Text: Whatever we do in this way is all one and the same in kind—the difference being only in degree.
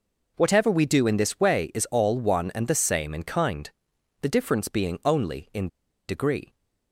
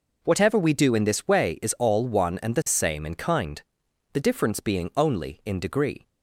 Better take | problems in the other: second | pauses between "in" and "degree"; at 5.6 s; 0.40 s long

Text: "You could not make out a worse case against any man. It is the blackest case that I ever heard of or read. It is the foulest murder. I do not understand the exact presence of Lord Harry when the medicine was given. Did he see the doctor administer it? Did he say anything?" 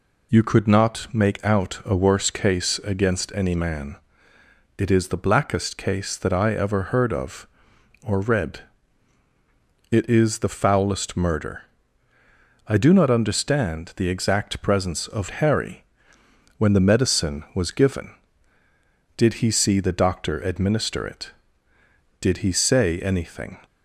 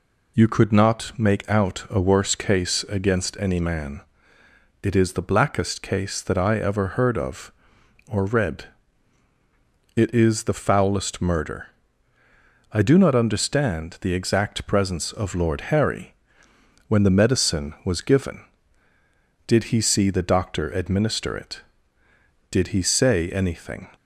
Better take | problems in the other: second | skips "Lord"; at 15.3 s // pauses between "Harry" and "when"; noticeable; at 15.8 s; 0.72 s long; noticeable in the second

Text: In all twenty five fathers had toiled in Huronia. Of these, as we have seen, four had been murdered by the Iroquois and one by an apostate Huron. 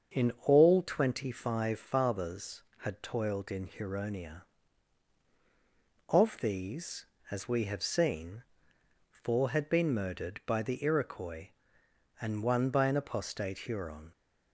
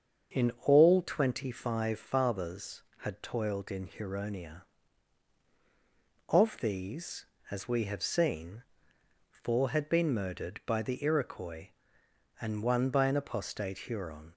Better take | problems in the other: neither | starts louder than the rest; the same in both

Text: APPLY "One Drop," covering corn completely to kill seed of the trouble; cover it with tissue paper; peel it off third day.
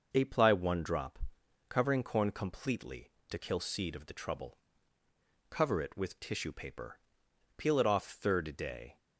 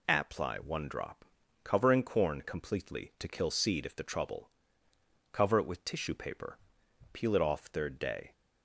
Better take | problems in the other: first | says "if" for "of"; at 3.8 s

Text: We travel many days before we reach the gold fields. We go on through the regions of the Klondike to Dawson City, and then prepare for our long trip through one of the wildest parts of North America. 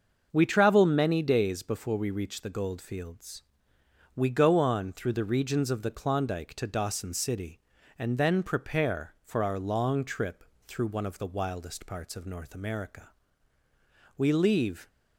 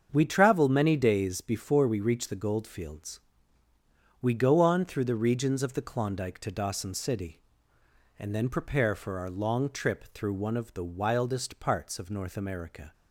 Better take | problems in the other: second | starts louder than the rest; until 1.3 s; 6.5 dB; strong in the second // pauses between "trip" and "through"; slight; at 10.4 s; 0.22 s long // goes on to say "We leave"; noticeable; from 14.1 s on; 0.70 s long

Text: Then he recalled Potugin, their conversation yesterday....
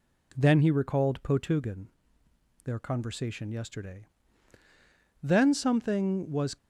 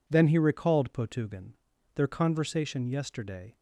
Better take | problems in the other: second | goes on to say "Then something was"; from 5.2 s on; 1.3 s long

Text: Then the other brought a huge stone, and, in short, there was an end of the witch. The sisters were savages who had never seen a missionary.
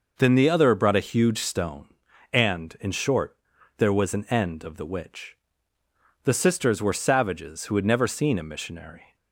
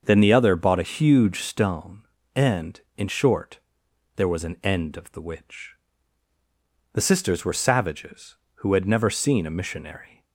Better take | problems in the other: first | starts louder than the rest; noticeable; until 1.0 s; 6 dB // says "bought" for "brought"; at 0.5 s

